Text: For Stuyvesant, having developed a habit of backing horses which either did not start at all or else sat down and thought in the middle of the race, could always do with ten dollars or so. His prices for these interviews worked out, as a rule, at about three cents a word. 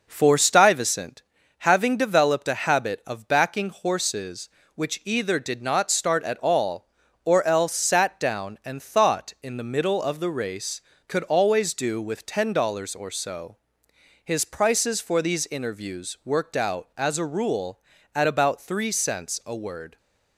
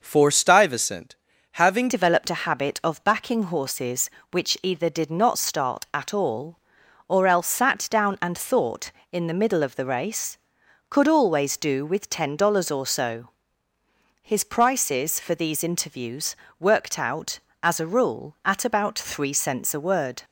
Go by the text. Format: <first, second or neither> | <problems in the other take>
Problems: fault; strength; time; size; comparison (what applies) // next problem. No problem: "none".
first | changes voice at "developed"; from 1.8 s on; 18.4 s long // pauses between "interviews" and "worked"; slight; at 16.3 s; 0.24 s long